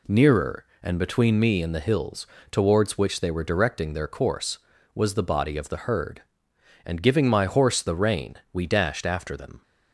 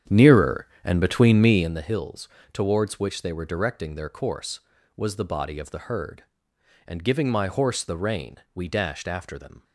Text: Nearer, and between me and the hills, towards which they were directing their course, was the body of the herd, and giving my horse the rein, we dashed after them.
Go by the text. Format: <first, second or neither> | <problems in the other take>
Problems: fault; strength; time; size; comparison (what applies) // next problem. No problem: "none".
first | starts louder than the rest; strong; until 1.8 s; 9 dB